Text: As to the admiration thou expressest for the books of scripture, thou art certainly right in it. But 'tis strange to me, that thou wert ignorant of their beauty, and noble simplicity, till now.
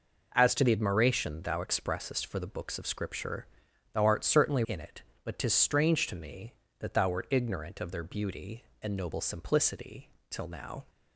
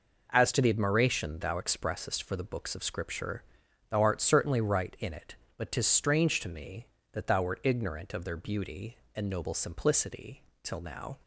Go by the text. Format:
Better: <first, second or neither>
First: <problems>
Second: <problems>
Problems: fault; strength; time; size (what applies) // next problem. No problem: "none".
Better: second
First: skips "right"; at 4.6 s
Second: none